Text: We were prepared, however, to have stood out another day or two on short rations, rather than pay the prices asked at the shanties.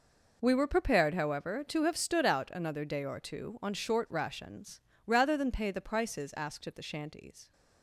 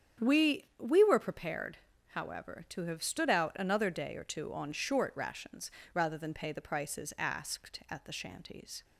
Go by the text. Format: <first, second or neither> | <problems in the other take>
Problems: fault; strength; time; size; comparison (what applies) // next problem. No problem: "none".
first | starts louder than the rest; strong; until 1.3 s; 8.5 dB // says "We" twice; at 0.8 s